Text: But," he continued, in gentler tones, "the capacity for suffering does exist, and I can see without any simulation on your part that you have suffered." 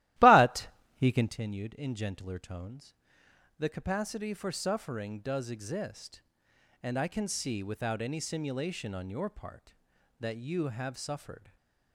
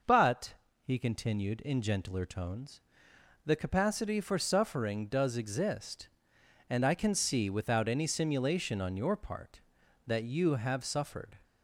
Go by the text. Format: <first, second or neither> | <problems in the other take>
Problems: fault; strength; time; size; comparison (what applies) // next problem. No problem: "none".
second | starts louder than the rest; strong; until 1.4 s; 15.5 dB // stays silent after the last word; slight; from 11.3 s on; 0.6 s long